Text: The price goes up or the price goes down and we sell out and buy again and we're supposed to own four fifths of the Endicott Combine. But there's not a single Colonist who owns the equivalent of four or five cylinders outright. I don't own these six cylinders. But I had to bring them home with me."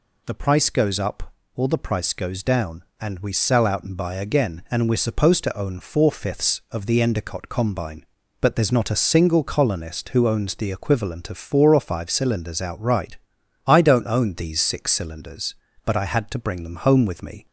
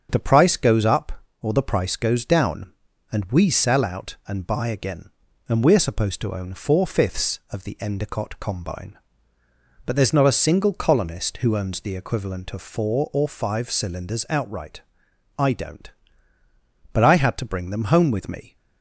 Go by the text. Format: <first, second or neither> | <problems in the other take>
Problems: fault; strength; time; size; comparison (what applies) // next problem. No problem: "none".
first | starts louder than the rest; until 1.1 s; 7 dB // skips "own these six cylinders"; at 16.4 s